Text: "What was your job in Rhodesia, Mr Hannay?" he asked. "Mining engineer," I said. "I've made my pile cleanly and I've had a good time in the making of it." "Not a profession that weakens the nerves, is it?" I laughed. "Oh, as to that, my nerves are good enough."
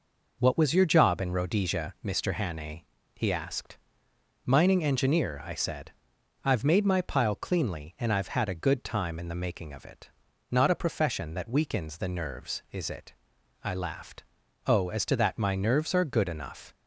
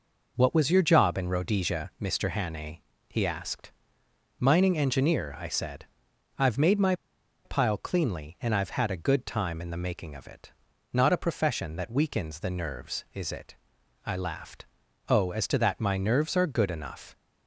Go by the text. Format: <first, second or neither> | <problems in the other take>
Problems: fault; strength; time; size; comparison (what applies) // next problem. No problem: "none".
first | pauses between "my" and "pile"; noticeable; at 6.9 s; 0.51 s long